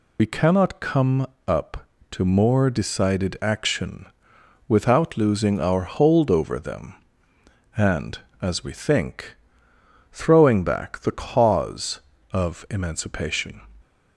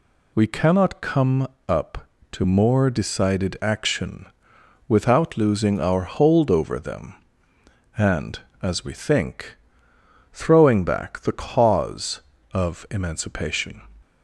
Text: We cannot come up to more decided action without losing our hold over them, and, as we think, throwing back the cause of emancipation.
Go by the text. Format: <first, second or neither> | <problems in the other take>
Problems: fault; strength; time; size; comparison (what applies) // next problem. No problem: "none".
second | loses the start of "We"; at 0.1 s; 65 ms // pauses between "come" and "up"; slight; at 1.2 s; 0.22 s long; slight in the second // pauses between "action" and "without"; noticeable; at 4.0 s; 0.62 s long; noticeable in the second